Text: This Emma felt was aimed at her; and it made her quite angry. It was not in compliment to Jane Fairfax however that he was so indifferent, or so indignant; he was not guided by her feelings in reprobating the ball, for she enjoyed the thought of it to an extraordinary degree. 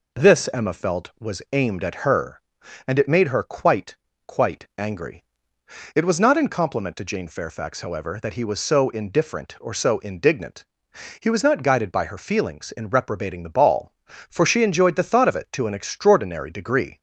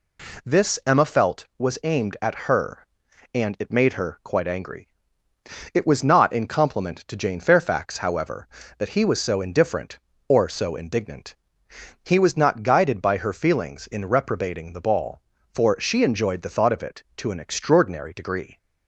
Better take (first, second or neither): second